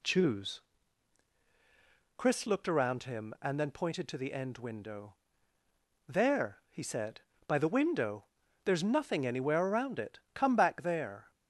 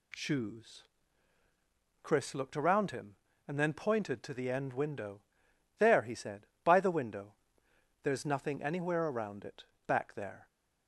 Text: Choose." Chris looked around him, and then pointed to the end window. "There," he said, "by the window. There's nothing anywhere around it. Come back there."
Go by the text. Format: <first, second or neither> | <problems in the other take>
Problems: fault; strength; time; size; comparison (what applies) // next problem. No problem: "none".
first | skips "Come"; at 9.7 s